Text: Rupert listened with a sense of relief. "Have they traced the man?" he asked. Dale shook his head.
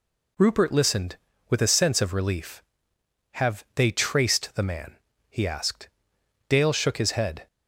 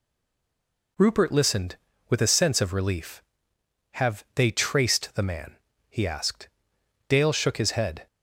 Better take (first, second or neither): first